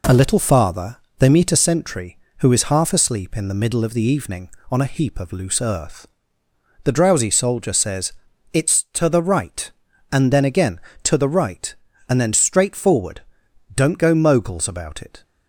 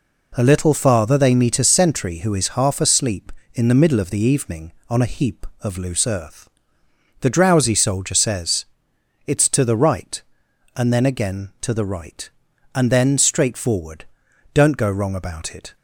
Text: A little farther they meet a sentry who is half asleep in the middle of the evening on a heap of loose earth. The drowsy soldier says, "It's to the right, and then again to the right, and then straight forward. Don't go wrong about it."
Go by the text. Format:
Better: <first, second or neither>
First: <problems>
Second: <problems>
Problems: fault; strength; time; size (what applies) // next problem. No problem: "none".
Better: second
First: pauses between "farther" and "they"; slight; at 0.9 s; 0.20 s long // says "moguls" for "wrong"; at 14.1 s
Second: none